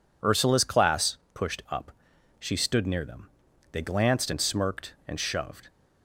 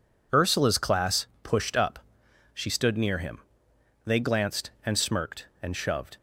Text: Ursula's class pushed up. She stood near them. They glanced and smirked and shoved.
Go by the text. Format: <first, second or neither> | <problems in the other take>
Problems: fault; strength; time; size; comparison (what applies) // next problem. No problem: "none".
first | pauses between "class" and "pushed"; slight; at 1.2 s; 0.16 s long; slight in the first // says "him" for "them"; at 3.1 s